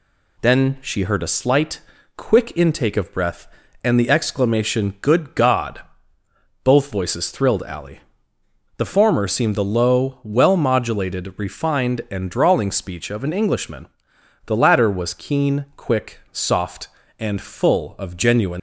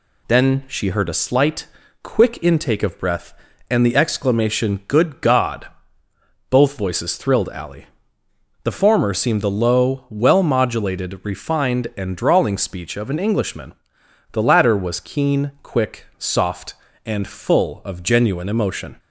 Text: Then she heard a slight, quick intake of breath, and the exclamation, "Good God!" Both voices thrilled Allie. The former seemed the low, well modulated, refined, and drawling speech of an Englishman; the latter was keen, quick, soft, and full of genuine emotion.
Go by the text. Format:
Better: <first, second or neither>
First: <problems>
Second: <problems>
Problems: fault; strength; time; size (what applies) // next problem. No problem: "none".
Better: second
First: stops before "emotion"; at 18.5 s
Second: none